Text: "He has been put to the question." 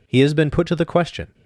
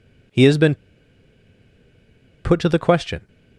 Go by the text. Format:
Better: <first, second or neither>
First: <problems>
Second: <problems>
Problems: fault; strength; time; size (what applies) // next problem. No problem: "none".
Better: first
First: none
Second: pauses between "been" and "put"; strong; at 0.7 s; 1.6 s long